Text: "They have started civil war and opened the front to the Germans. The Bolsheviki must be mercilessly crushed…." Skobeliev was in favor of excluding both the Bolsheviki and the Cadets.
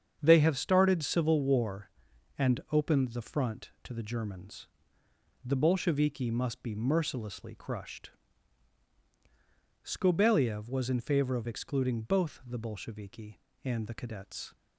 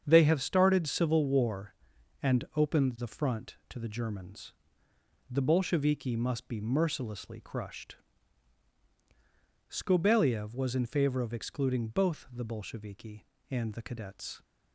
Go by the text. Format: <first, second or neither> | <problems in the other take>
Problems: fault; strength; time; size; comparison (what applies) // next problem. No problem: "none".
neither | starts louder than the rest; strong; the same in both